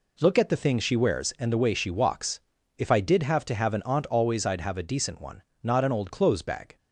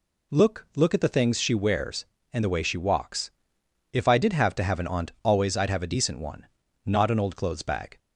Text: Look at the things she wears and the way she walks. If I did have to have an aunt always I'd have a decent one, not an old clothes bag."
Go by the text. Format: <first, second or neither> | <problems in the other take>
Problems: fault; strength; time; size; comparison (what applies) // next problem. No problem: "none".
first | says "Look" twice; at 0.7 s